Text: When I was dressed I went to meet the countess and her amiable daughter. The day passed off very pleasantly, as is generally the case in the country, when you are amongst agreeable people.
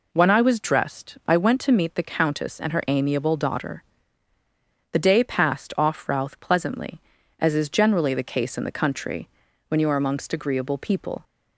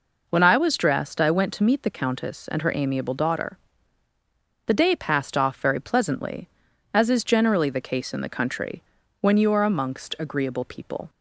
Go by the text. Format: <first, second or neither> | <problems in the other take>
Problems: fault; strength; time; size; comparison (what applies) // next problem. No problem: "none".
second | says "routh" for "very"; at 6.0 s